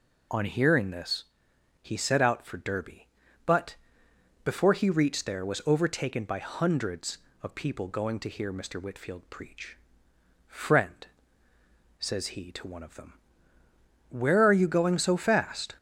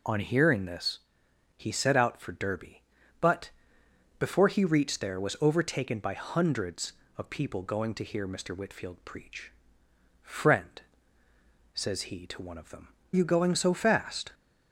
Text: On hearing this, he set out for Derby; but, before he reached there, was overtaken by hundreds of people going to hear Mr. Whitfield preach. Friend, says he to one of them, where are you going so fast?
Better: first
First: none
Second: skips "where are"; at 13.0 s

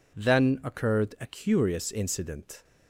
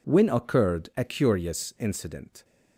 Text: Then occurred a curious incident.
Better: first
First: none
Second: says "When" for "Then"; at 0.0 s

